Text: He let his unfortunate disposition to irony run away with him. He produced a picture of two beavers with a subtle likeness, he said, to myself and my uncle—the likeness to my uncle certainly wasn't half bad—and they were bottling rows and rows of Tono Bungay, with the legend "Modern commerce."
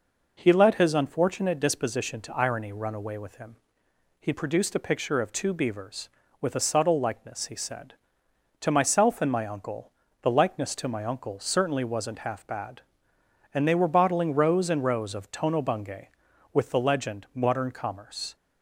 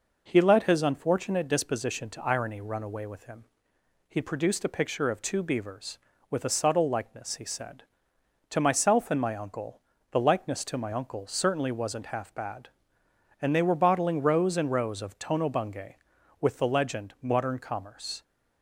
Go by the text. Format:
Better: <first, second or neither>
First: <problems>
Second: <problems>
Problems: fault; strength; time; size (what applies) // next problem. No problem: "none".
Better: neither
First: none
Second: none